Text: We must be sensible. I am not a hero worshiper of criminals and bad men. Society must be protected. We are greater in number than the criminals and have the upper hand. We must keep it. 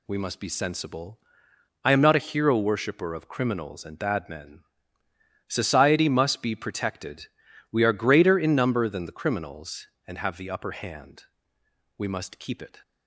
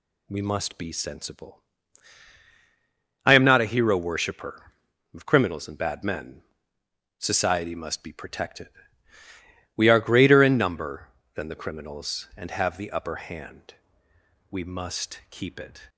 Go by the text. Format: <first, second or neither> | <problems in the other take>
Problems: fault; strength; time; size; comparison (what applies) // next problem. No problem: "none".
neither | none